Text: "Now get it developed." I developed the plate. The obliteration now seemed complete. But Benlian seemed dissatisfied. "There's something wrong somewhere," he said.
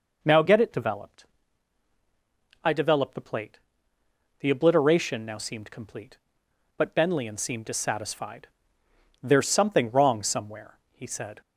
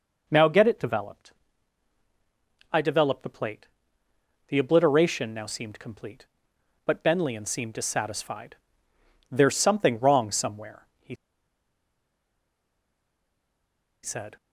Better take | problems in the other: first | pauses between "he" and "said"; strong; at 11.1 s; 2.8 s long

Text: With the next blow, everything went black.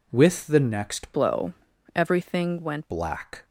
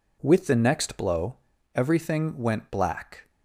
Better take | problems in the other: second | changes voice from "blow" to "went"; from 1.1 to 2.9 s; 1.8 s long

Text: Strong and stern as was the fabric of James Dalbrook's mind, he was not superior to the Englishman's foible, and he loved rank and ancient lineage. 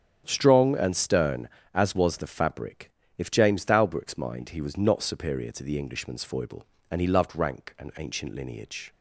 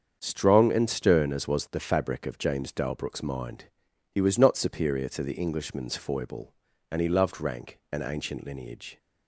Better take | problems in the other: second | starts louder than the rest; strong; until 1.2 s; 8.5 dB; strong in the second // says "if" for "of"; at 3.1 s

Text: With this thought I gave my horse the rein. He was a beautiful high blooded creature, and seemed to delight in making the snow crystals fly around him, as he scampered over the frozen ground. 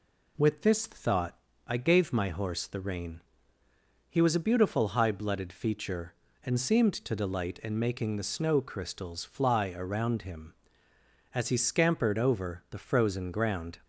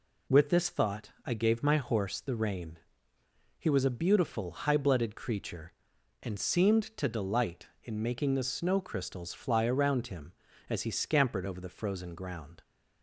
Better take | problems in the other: second | pauses between "thought" and "I"; slight; at 1.3 s; 0.32 s long // says "feature" for "creature"; at 5.4 s

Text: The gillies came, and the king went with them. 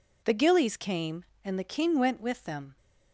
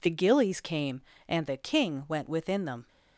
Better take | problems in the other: first | says "within" for "with"; at 2.2 s

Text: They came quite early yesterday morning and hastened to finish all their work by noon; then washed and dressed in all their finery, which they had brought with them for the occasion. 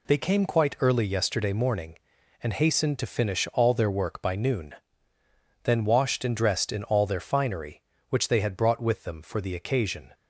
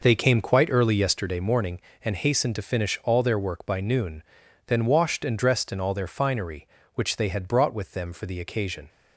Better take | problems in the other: first | starts louder than the rest; noticeable; until 1.2 s; 5.5 dB

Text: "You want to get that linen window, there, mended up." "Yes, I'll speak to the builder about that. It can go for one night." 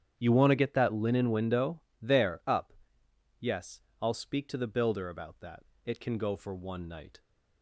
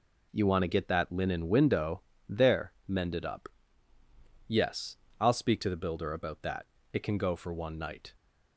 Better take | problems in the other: second | starts louder than the rest; strong; until 1.1 s; 9.5 dB // skips "mended"; at 2.4 s

